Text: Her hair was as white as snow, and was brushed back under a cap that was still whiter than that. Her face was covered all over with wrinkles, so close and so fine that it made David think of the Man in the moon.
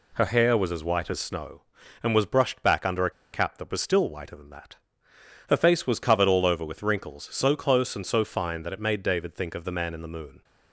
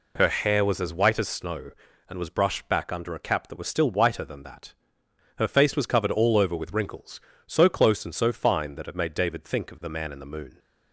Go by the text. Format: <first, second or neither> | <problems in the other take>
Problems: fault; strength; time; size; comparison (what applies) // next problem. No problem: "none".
second | pauses between "a" and "cap"; slight; at 3.0 s; 0.23 s long